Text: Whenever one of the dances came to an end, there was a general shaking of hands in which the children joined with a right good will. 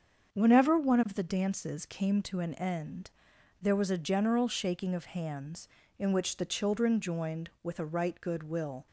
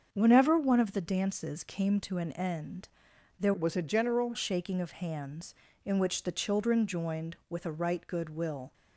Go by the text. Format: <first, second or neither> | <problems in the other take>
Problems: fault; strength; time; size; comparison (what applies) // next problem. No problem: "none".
first | starts louder than the rest; until 1.1 s; 6.5 dB; also in the first // changes voice from "was" to "general"; from 3.5 to 4.3 s; 0.8 s long